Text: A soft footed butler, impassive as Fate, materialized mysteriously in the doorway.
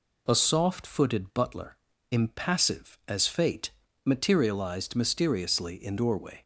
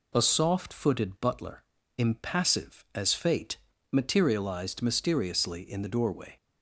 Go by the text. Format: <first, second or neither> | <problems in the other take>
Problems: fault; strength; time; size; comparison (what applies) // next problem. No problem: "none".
second | skips "the"; at 5.9 s